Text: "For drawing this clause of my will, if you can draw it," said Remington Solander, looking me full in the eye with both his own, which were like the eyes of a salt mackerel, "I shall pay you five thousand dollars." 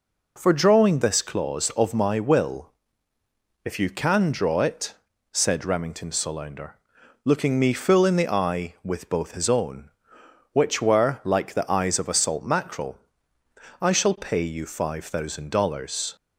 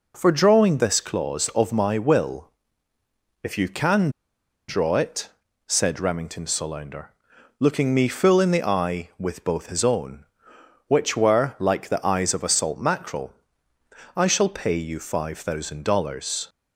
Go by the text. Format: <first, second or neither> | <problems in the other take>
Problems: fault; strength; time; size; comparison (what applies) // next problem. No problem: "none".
first | pauses between "can" and "draw"; noticeable; at 4.0 s; 0.58 s long